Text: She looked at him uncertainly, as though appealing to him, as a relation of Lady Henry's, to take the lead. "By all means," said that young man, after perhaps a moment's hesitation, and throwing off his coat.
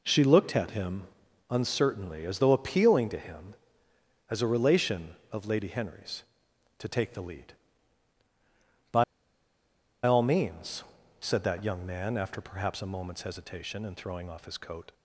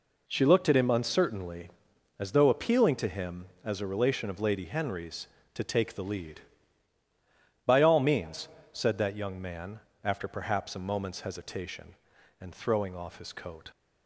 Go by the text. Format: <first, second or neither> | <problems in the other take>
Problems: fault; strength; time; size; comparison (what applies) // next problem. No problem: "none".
second | pauses between "him" and "uncertainly"; noticeable; at 1.0 s; 0.46 s long // pauses between "By" and "all"; at 9.0 s; 1.0 s long